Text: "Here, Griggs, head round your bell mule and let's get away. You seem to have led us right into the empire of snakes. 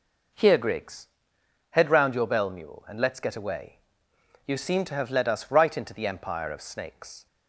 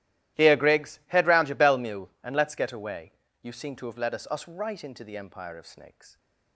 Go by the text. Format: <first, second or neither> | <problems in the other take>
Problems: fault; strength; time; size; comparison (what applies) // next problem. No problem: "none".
first | starts louder than the rest; strong; until 1.4 s; 14.5 dB // says "us" twice; at 4.2 s